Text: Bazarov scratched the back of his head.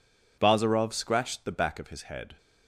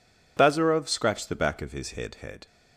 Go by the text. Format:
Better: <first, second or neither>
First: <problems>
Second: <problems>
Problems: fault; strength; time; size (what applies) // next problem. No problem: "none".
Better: first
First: none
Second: says "head" twice; at 2.1 s